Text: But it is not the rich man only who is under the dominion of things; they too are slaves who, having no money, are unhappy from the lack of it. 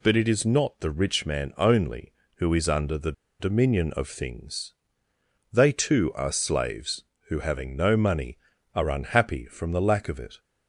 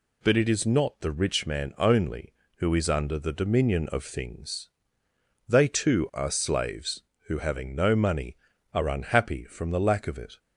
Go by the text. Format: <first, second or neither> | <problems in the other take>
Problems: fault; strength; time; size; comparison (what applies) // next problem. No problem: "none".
second | pauses between "the" and "dominion"; slight; at 3.1 s; 0.27 s long